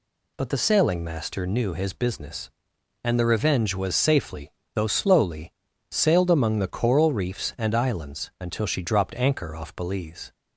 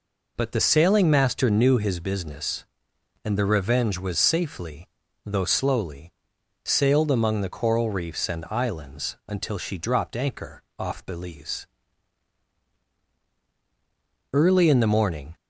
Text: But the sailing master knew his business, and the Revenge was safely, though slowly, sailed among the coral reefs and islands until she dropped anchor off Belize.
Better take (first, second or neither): first